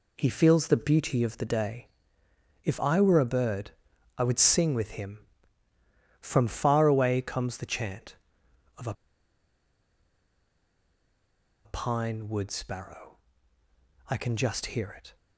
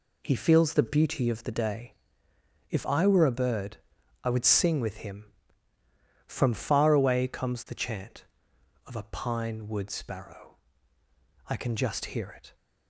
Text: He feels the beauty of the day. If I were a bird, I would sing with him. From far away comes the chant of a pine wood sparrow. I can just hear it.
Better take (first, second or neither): second